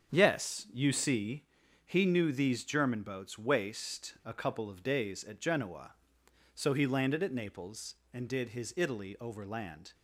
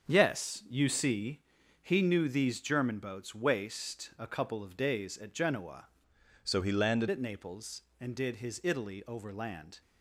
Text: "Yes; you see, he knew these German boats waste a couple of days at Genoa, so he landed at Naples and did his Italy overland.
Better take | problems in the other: first | starts louder than the rest; strong; until 1.1 s; 7.5 dB; strong in the first // changes voice from "so" to "landed"; from 6.4 to 7.0 s; 0.6 s long

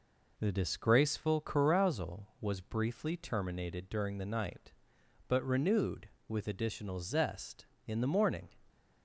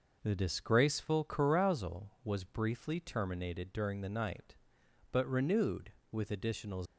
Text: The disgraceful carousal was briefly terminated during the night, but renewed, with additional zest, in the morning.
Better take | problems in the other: first | stops before "zest in the morning"; at 6.8 s

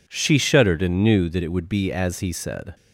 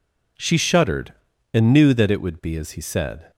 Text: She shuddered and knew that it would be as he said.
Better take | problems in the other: neither | none

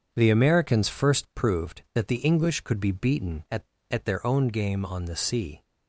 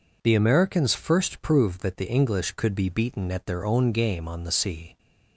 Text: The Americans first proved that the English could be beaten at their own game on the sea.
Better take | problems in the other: second | starts louder than the rest; until 1.1 s; 7 dB // says "at" twice; at 3.8 s

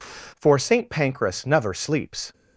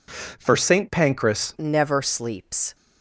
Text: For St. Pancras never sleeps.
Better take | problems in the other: first | changes voice at "never"; from 1.5 s on; 1.2 s long

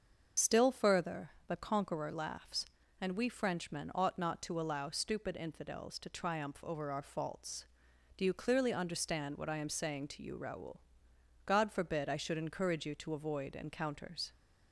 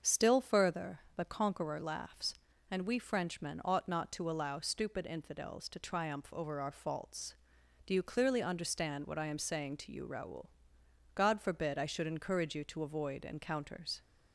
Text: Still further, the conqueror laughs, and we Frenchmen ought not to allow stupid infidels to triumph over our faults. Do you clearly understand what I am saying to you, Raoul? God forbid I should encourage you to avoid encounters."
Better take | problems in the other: second | loses the start of "Still"; at 0.3 s; 35 ms // starts louder than the rest; until 1.5 s; 7 dB; also in the second

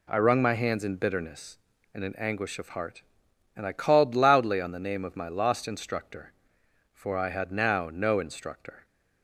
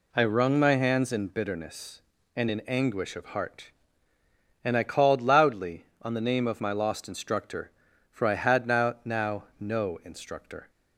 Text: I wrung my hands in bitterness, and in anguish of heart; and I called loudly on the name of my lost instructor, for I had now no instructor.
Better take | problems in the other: first | says "now" twice; at 9.0 s

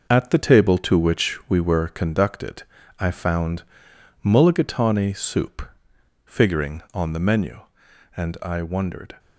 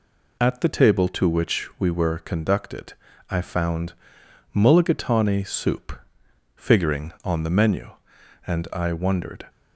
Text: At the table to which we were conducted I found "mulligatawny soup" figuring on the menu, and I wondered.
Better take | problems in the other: second | gets quieter; throughout; 7 dB // pauses between "conducted" and "I"; slight; at 2.6 s; 0.36 s long; slight in the second // pauses between "found" and "mulligatawny"; noticeable; at 3.6 s; 0.60 s long; noticeable in the second // pauses between "soup" and "figuring"; noticeable; at 5.6 s; 0.60 s long; noticeable in the second

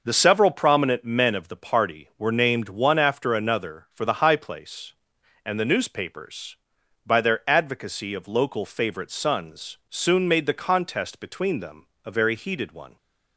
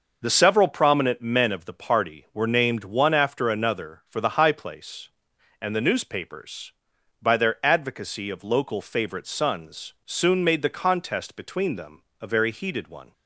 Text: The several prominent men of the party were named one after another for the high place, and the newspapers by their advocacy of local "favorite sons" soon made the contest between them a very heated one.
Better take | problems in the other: neither | pauses between "them" and "a"; slight; the same in both

